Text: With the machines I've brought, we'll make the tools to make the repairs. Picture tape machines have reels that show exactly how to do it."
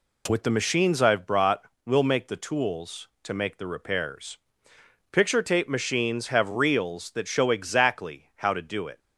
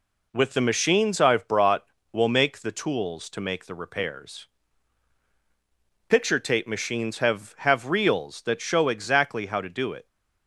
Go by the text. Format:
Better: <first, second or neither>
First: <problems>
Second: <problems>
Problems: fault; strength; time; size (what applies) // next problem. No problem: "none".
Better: first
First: none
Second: says "have" twice; at 7.5 s